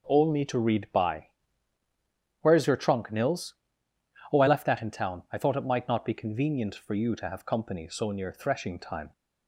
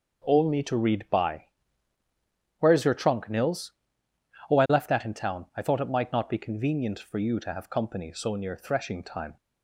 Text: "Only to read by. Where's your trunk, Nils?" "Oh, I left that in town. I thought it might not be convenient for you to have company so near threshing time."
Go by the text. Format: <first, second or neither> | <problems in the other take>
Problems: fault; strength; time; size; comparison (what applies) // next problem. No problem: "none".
neither | none